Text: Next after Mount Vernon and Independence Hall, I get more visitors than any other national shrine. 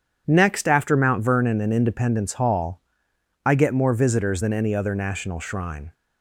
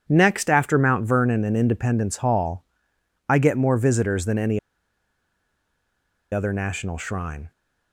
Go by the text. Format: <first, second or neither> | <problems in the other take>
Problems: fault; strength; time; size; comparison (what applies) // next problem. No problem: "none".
first | starts louder than the rest; strong; until 1.0 s; 8.5 dB; strong in the first // pauses between "any" and "other"; strong; at 4.5 s; 1.7 s long